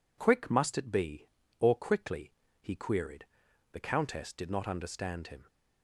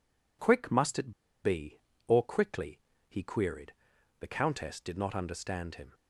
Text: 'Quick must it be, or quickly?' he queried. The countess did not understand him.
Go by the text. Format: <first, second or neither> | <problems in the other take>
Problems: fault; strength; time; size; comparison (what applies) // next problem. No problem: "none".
first | pauses between "it" and "be"; slight; at 1.1 s; 0.32 s long